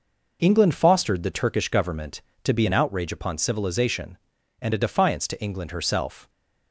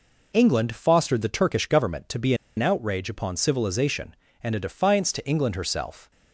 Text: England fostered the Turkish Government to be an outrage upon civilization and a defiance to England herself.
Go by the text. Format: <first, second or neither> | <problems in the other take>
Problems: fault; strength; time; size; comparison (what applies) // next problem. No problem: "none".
first | pauses between "be" and "an"; slight; at 2.3 s; 0.22 s long